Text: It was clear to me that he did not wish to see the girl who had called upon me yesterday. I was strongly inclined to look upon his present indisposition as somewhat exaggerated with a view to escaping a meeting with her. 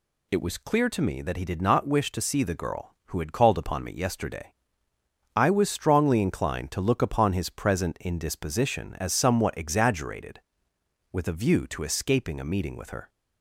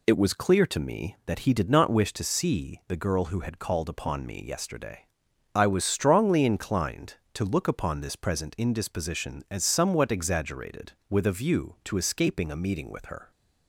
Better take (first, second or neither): first